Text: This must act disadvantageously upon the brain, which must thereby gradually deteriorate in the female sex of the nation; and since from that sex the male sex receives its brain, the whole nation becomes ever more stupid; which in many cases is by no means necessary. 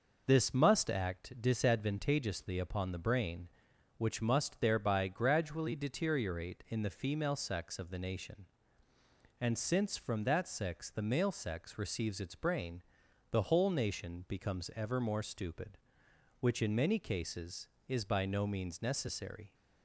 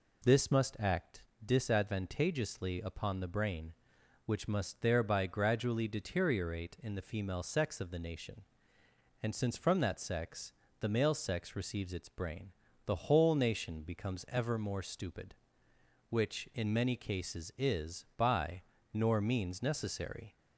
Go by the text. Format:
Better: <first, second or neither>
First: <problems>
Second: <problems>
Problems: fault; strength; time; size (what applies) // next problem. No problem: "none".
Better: first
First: none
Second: pauses between "act" and "disadvantageously"; slight; at 1.2 s; 0.22 s long // pauses between "sex" and "the"; slight; at 10.5 s; 0.26 s long // says "nor" for "no"; at 18.9 s